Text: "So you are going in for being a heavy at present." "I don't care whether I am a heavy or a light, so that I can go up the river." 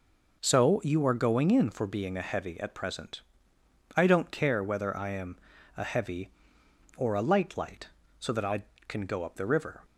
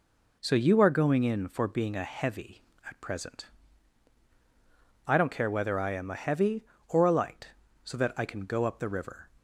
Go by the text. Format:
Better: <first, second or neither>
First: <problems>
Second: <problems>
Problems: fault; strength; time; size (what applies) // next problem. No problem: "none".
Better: second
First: pauses between "am" and "a"; at 5.3 s; 0.40 s long // says "light" twice; at 7.5 s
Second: none